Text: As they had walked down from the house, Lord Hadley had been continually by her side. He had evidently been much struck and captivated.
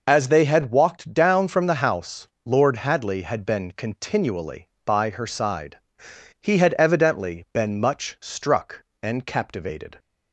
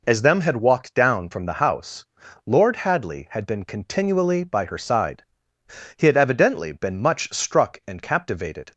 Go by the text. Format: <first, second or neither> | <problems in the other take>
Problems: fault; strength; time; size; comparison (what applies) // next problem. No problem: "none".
first | says "them" for "they"; at 0.2 s